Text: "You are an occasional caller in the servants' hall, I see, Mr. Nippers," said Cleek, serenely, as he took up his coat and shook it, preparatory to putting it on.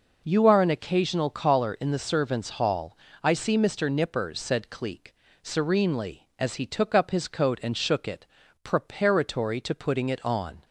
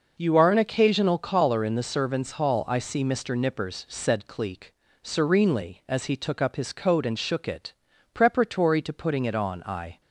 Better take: first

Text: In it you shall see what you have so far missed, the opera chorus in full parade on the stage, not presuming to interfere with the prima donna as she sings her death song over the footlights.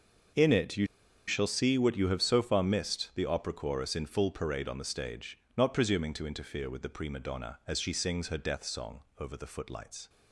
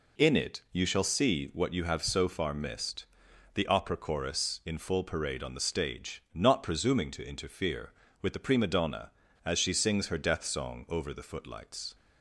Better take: second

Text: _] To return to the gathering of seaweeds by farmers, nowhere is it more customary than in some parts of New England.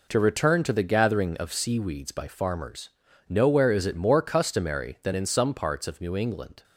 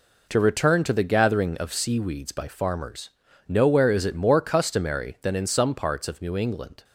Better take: neither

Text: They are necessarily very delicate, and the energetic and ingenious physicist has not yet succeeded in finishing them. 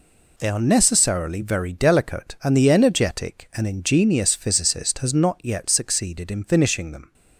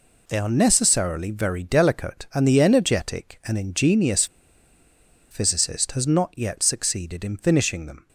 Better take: first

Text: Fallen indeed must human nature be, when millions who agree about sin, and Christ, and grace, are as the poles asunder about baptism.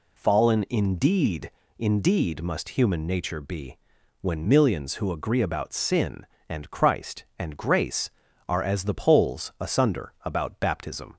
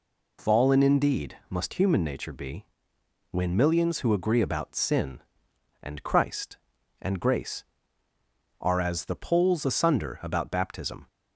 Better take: second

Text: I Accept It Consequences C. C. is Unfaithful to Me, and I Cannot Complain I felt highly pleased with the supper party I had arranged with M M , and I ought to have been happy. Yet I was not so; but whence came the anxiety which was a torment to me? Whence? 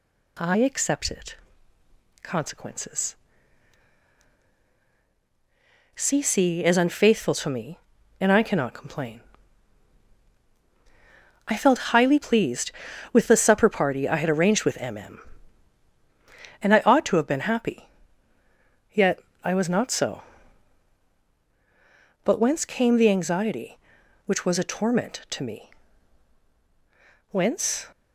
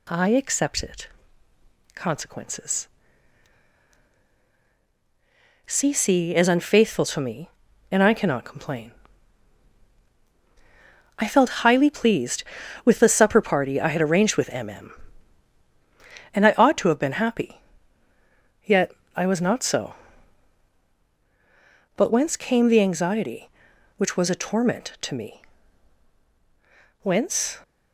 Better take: neither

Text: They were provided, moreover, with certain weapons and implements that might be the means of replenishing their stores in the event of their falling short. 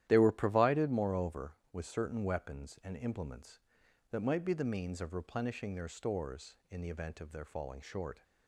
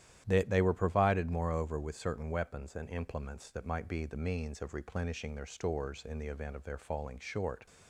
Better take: first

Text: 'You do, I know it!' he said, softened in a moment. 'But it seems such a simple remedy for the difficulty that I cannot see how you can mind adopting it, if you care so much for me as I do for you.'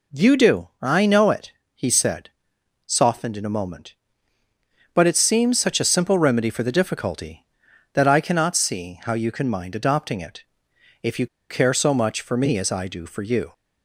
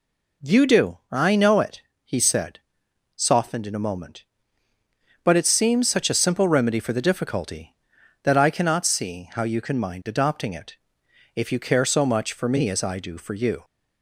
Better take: second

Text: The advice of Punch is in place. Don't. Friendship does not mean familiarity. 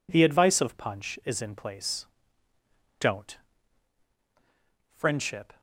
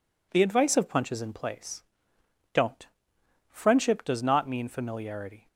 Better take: second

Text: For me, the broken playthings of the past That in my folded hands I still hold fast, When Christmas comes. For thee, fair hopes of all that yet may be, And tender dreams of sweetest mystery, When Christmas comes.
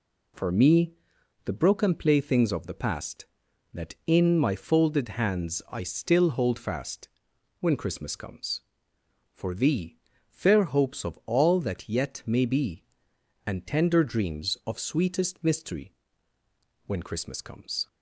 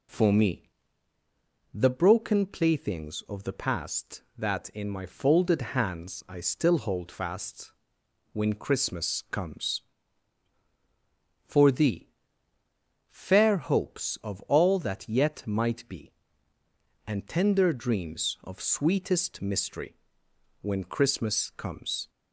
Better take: first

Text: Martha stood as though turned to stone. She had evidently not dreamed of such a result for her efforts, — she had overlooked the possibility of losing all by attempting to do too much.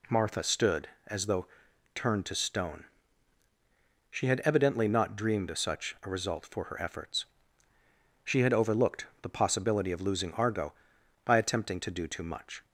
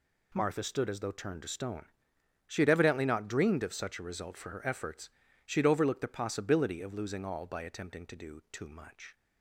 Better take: second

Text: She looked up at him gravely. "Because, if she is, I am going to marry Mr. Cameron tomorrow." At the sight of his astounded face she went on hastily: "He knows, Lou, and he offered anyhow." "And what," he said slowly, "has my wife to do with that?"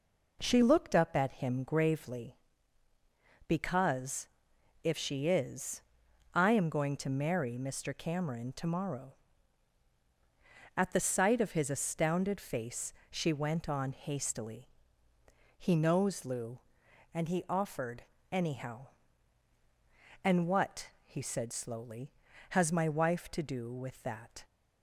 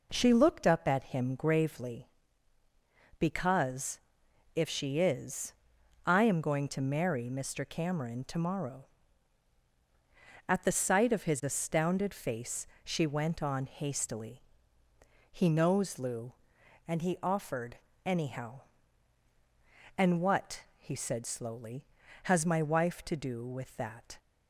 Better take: neither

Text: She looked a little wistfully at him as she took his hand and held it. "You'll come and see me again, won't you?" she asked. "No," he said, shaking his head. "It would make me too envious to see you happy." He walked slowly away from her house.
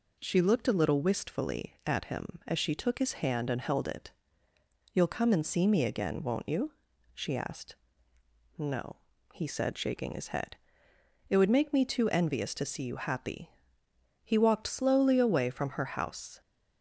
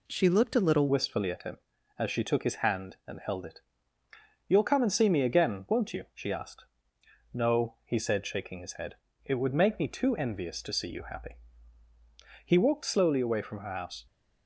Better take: first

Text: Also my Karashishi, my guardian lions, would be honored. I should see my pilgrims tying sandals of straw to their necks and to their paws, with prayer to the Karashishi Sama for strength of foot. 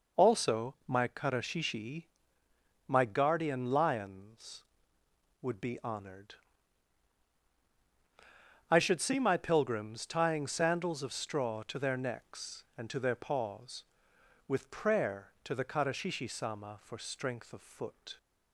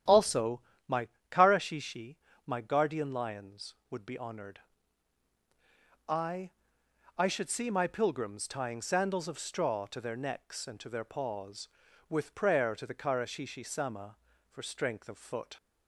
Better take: first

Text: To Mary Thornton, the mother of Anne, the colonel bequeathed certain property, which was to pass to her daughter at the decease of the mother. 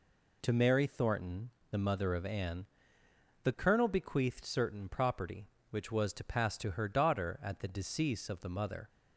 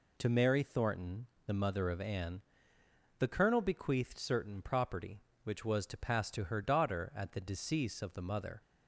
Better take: neither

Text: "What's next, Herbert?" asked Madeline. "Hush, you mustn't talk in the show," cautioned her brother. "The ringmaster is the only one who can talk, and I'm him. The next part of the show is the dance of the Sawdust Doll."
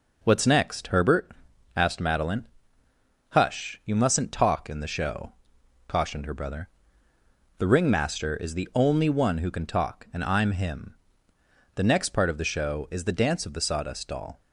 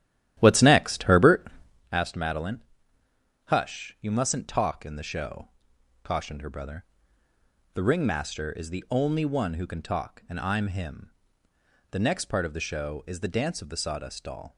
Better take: first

